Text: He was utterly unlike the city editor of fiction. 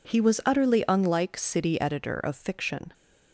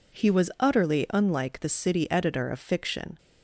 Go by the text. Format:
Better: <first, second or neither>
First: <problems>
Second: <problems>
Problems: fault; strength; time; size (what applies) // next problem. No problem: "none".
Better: second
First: skips "the"; at 1.3 s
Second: none